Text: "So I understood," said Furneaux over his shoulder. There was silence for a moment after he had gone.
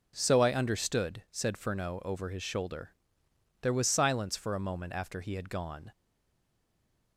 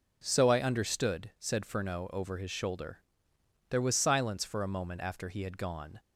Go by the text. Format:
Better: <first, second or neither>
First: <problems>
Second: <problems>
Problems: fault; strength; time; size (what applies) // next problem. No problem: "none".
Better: second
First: stays silent after the last word; noticeable; from 5.9 s on; 1.2 s long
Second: none